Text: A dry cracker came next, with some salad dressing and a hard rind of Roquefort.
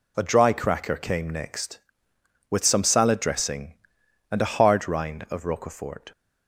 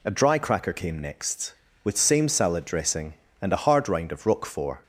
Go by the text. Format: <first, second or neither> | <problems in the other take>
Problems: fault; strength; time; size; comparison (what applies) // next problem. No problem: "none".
first | says "same" for "some"; at 1.9 s